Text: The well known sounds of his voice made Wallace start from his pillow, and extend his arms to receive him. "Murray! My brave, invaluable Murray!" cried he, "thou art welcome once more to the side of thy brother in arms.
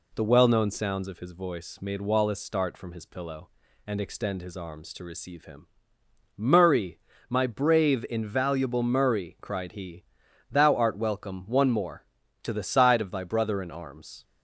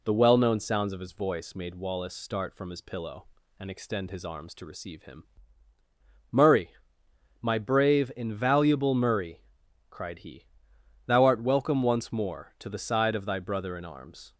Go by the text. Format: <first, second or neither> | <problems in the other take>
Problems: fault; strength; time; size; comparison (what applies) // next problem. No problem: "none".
second | says "one" for "once"; at 11.4 s